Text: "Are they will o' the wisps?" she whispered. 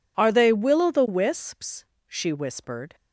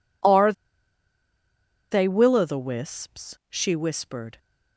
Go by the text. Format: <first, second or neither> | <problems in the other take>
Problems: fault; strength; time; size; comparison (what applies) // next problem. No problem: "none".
first | pauses between "Are" and "they"; strong; at 0.5 s; 1.3 s long